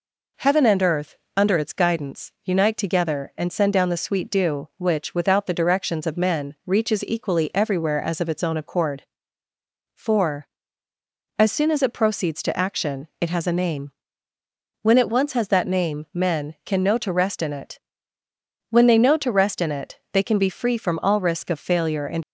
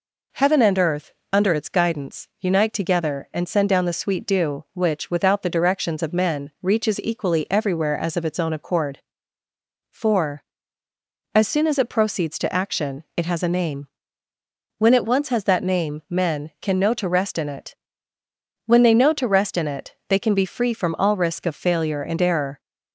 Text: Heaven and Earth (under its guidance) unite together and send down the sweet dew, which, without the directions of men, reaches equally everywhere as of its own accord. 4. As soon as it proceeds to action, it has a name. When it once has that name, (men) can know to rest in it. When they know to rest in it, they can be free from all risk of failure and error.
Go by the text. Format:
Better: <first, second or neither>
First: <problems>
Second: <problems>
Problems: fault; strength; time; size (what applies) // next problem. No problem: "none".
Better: second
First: stops before "error"; at 22.2 s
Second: none